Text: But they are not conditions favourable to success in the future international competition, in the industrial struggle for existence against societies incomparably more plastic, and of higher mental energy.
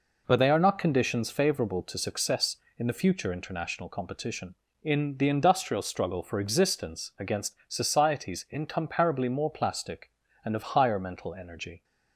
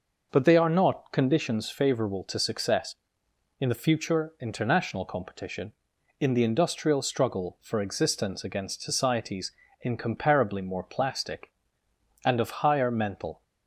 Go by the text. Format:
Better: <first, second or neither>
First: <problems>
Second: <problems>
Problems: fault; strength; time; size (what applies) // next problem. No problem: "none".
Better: first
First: none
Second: pauses between "societies" and "incomparably"; slight; at 9.5 s; 0.30 s long // stops before "energy"; at 13.4 s